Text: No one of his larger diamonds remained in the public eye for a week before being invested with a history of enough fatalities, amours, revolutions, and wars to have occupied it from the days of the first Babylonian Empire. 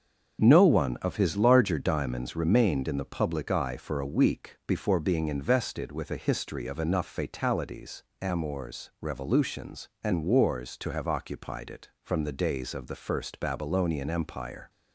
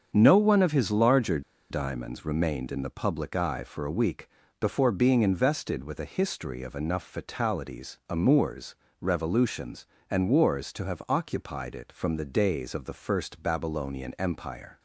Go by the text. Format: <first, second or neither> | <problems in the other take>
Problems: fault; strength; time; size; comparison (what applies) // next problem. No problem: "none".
first | starts louder than the rest; strong; until 1.1 s; 7 dB; strong in the first // pauses between "larger" and "diamonds"; slight; at 1.3 s; 0.30 s long // pauses between "week" and "before"; slight; at 4.2 s; 0.32 s long